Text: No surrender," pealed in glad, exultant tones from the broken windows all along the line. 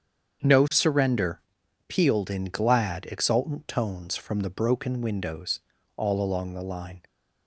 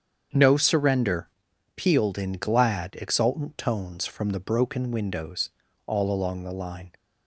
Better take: neither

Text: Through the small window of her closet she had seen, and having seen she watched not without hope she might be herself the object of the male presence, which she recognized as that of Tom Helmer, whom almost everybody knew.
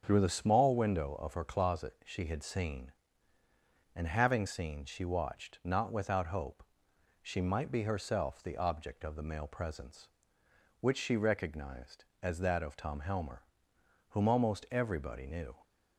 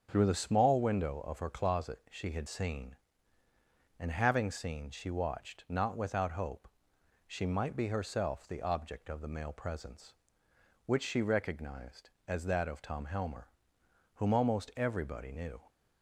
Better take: neither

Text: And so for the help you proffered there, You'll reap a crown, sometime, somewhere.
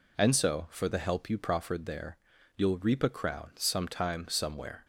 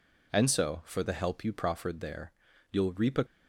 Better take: first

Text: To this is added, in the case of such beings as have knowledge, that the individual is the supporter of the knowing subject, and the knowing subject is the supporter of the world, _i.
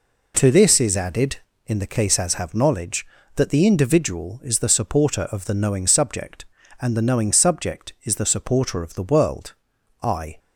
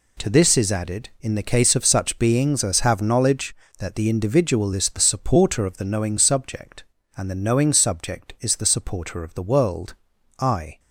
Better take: second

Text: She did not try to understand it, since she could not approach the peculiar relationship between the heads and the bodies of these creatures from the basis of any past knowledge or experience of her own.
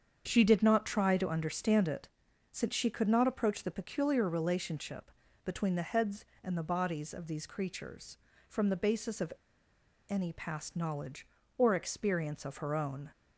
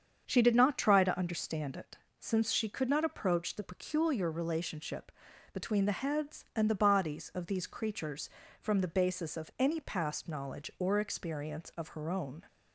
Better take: second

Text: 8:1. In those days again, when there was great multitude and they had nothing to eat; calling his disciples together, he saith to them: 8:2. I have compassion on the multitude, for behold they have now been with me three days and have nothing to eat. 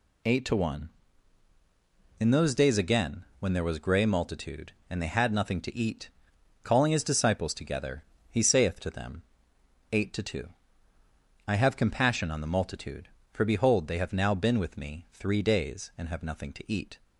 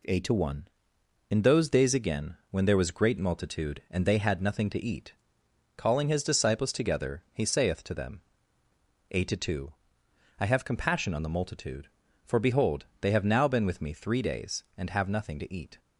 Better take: second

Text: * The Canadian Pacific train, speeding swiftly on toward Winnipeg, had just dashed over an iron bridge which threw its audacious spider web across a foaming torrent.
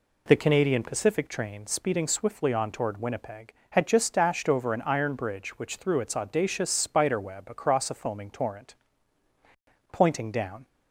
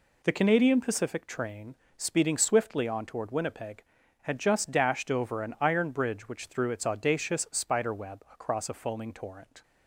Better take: second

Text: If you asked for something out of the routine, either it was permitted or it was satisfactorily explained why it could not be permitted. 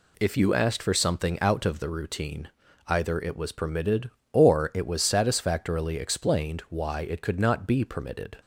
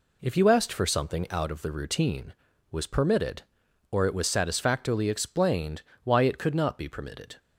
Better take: first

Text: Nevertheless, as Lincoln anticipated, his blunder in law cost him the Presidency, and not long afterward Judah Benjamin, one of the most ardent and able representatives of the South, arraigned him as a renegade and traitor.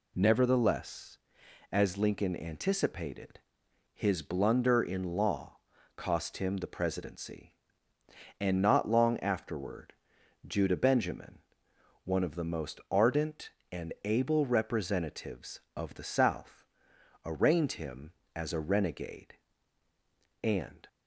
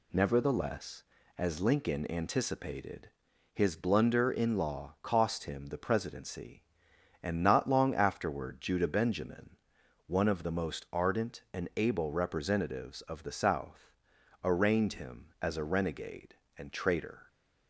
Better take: second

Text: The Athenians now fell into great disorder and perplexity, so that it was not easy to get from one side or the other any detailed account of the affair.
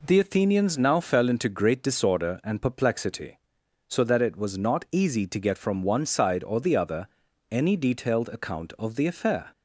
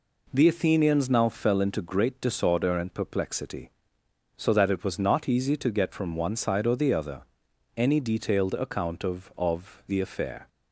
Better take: first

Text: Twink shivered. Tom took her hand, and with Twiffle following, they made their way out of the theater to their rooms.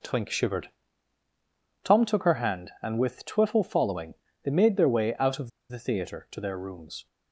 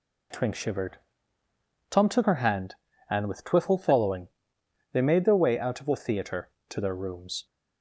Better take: second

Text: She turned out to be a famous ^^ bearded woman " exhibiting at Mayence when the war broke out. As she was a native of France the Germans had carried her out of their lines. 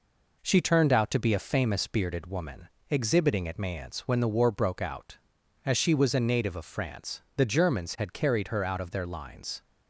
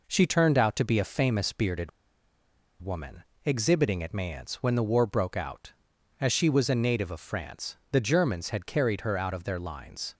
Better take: first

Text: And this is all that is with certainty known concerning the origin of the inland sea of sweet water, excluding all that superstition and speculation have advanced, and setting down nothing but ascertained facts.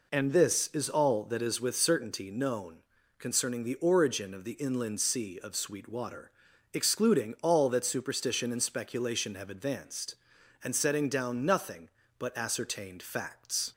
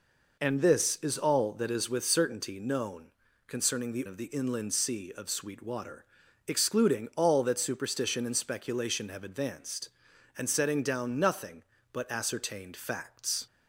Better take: first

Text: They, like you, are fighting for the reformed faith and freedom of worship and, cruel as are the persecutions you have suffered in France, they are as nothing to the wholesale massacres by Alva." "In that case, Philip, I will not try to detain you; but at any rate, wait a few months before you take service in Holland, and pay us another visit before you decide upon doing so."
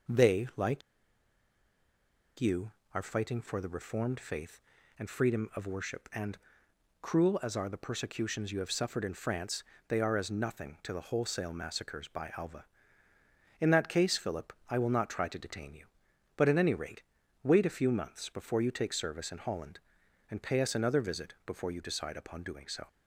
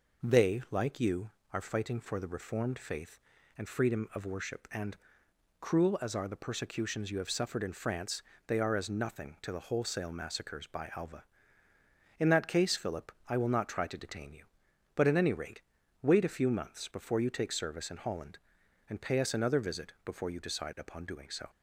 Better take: second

